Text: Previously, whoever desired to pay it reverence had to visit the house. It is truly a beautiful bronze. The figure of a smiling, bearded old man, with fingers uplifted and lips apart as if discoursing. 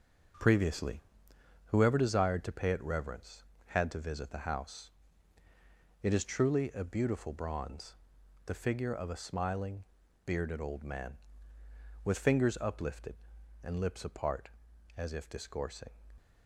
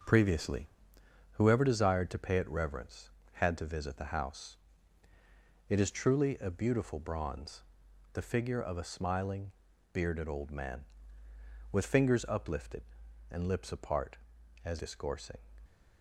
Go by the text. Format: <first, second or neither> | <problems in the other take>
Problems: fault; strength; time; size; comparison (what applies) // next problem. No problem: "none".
first | starts louder than the rest; noticeable; until 1.7 s; 6 dB // skips "if"; at 14.7 s